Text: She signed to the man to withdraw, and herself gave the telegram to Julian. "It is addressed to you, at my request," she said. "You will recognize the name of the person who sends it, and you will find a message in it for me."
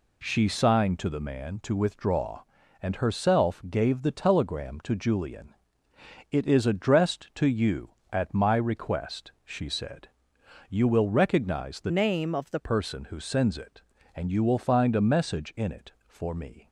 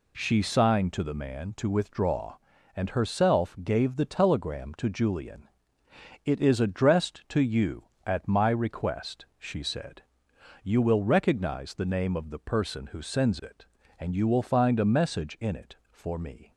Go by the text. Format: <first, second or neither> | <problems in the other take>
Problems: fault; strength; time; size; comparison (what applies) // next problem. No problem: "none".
second | changes voice from "name" to "the"; from 11.9 to 12.5 s; 0.6 s long